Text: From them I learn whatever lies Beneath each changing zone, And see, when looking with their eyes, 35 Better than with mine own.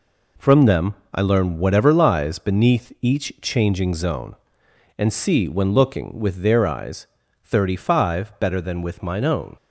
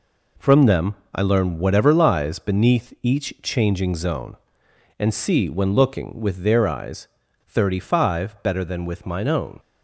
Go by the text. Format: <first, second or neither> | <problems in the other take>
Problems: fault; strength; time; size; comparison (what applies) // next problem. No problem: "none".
neither | pauses between "them" and "I"; slight; the same in both